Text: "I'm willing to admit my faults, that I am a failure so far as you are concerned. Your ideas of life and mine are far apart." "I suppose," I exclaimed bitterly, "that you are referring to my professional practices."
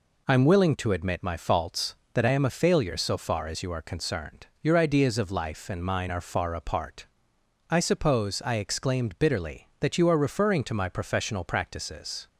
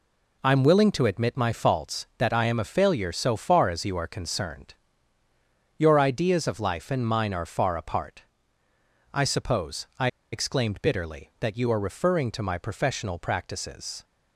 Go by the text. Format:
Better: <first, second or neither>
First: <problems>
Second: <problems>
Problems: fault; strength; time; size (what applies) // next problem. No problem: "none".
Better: first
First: none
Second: pauses between "I" and "exclaimed"; slight; at 10.0 s; 0.25 s long